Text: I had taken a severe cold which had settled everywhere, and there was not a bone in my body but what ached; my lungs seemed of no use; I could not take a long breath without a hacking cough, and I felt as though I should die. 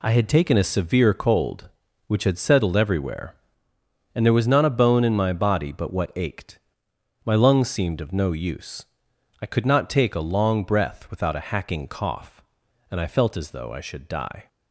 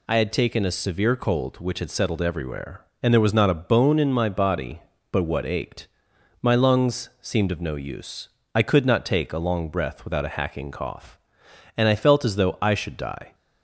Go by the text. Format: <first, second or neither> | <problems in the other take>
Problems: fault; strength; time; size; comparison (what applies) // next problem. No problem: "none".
neither | none